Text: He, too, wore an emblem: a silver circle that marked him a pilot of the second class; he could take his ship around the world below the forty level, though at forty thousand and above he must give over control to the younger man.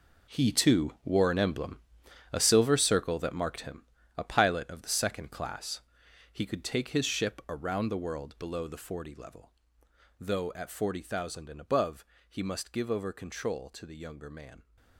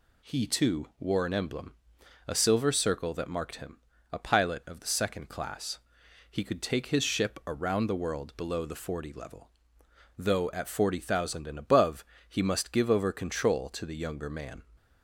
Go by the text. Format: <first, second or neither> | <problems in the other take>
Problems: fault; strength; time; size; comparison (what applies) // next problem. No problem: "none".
second | gets quieter; strong; throughout; 13.5 dB // pauses between "him" and "a"; slight; at 3.8 s; 0.32 s long; slight in the second // pauses between "above" and "he"; slight; at 12.0 s; 0.24 s long; slight in the second